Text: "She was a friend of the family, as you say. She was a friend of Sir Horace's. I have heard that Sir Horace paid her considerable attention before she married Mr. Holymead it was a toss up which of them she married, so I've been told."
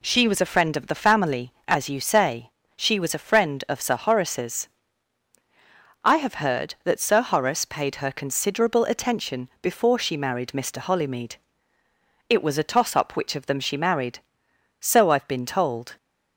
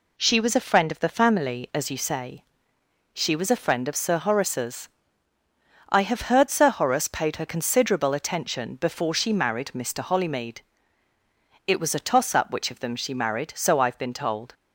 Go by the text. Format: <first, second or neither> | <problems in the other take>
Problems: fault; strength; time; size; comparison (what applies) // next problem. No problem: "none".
first | skips "that"; at 6.4 s // pauses between "Holymead" and "it"; at 10.6 s; 1.0 s long; noticeable in the first